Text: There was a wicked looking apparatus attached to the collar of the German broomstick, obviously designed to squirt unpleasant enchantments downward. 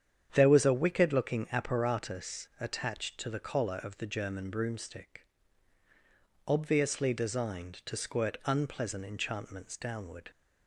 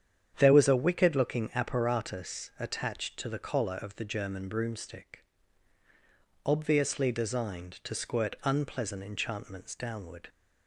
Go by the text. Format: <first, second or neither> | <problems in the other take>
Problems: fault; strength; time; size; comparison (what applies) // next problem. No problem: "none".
neither | starts louder than the rest; strong; the same in both